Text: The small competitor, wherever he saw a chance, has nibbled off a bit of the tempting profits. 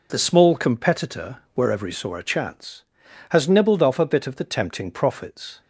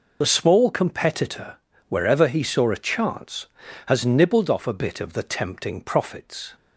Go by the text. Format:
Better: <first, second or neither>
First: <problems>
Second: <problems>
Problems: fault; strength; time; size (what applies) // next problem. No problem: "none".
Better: first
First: none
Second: loses the start of "The"; at 0.2 s; 35 ms